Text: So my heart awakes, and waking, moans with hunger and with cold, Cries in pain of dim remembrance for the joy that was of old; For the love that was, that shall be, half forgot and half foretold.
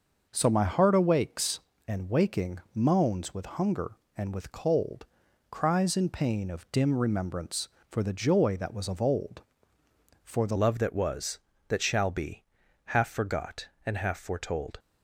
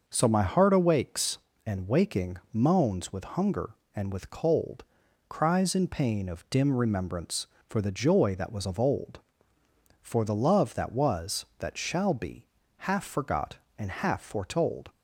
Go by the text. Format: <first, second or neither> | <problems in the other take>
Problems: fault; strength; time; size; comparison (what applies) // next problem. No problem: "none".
second | changes voice at "love"; from 10.5 s on; 4.2 s long